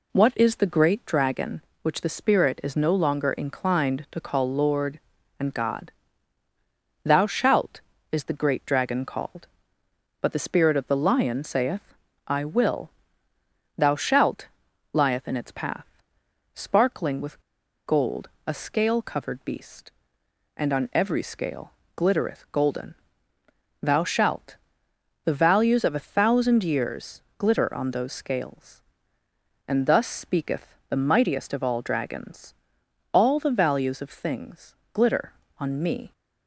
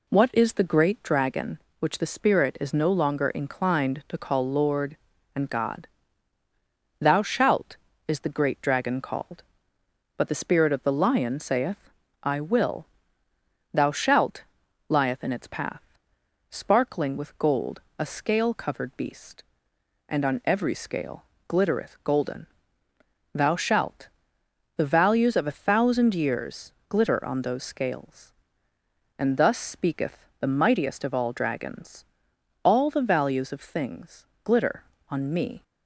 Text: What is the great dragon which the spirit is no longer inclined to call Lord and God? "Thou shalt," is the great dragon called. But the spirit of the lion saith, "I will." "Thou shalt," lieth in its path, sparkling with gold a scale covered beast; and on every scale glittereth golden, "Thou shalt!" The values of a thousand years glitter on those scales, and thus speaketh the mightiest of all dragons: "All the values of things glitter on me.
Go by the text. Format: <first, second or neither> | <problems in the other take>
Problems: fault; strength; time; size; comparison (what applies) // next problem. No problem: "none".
second | pauses between "with" and "gold"; noticeable; at 17.3 s; 0.46 s long // pauses between "gold" and "a"; slight; at 18.2 s; 0.18 s long; slight in the second // pauses between "scale" and "glittereth"; slight; at 21.7 s; 0.24 s long; slight in the second // pauses between "years" and "glitter"; slight; at 27.2 s; 0.16 s long; slight in the second // pauses between "speaketh" and "the"; slight; at 30.7 s; 0.16 s long; slight in the second // pauses between "things" and "glitter"; slight; at 34.7 s; 0.16 s long; slight in the second